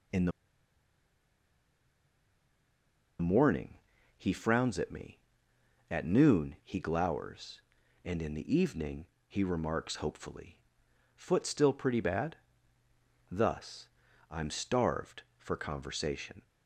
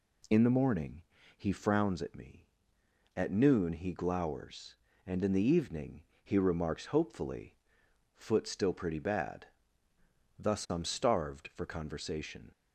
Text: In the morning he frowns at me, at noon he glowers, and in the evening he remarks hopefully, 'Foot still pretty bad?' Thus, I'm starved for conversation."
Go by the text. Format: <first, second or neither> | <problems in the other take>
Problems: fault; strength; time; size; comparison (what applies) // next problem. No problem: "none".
second | pauses between "the" and "morning"; strong; at 0.3 s; 2.8 s long // pauses between "morning" and "he"; at 3.7 s; 0.42 s long; slight in the second // pauses between "evening" and "he"; slight; at 9.0 s; 0.22 s long; slight in the second